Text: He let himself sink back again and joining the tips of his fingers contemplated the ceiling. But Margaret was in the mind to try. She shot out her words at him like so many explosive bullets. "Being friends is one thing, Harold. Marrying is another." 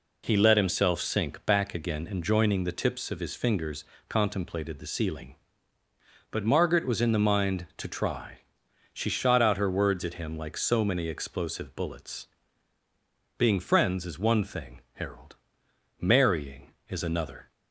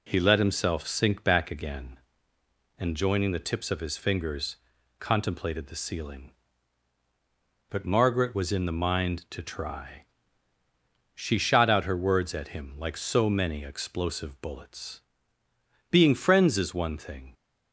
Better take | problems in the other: first | pauses between "fingers" and "contemplated"; at 4.5 s; 0.44 s long; slight in the first // stops before "Harold Marrying is another"; at 17.3 s

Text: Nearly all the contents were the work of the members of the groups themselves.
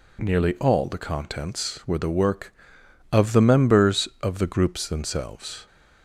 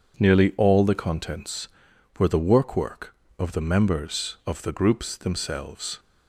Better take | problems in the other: first | says "work" twice; at 2.7 s

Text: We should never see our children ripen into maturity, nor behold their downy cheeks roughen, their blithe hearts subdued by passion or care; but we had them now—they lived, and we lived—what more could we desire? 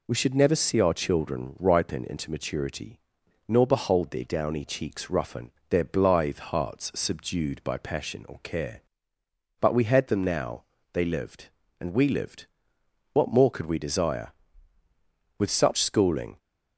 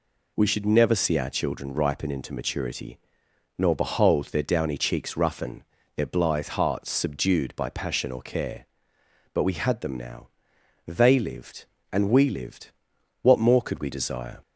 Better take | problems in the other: second | goes on to say "With such schooling"; noticeable; from 15.3 s on; 1.0 s long

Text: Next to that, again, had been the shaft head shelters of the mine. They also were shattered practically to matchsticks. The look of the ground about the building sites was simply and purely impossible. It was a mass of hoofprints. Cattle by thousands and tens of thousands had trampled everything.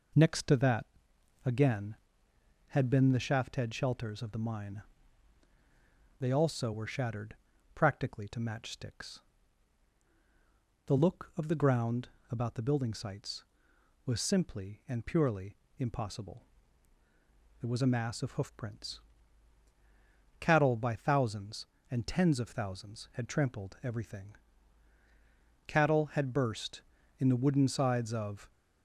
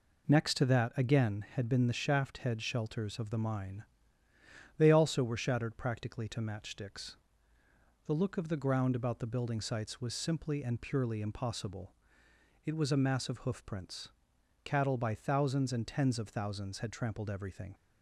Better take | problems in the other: second | pauses between "shattered" and "practically"; at 7.3 s; 0.40 s long // pauses between "ground" and "about"; slight; at 12.0 s; 0.20 s long // pauses between "purely" and "impossible"; slight; at 15.5 s; 0.22 s long // goes on to say "Cattle had burst in the wooden sides of"; strong; from 25.6 s on; 2.8 s long

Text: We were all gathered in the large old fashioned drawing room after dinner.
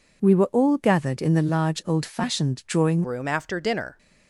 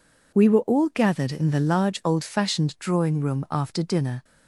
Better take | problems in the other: second | changes voice at "room"; from 3.0 s on; 0.9 s long

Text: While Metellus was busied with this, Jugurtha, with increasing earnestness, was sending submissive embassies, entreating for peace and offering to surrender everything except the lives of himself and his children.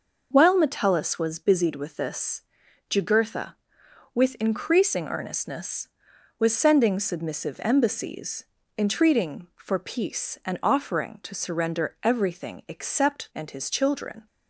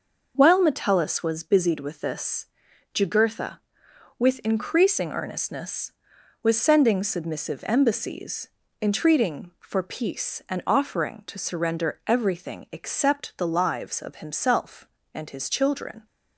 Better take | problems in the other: second | skips "the lives of himself"; at 13.3 s

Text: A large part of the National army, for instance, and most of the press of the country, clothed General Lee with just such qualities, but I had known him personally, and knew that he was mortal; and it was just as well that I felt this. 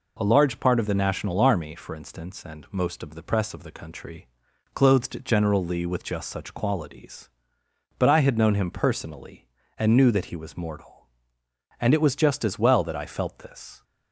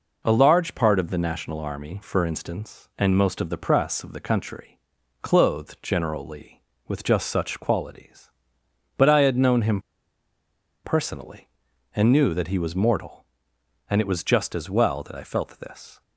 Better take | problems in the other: first | pauses between "him" and "personally"; at 9.7 s; 1.0 s long

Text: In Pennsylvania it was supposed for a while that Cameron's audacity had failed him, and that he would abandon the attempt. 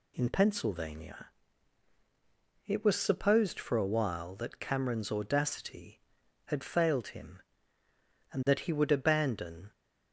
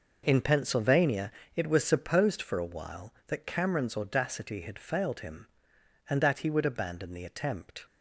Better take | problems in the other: second | pauses between "Pennsylvania" and "it"; strong; at 1.2 s; 1.3 s long; slight in the second // stops before "the attempt"; at 9.7 s

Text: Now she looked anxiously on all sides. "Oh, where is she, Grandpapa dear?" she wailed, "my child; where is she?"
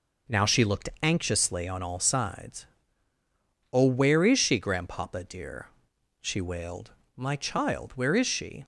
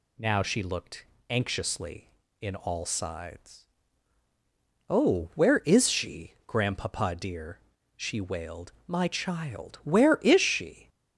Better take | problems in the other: first | pauses between "looked" and "anxiously"; slight; at 1.0 s; 0.24 s long // says "in" for "on"; at 2.4 s

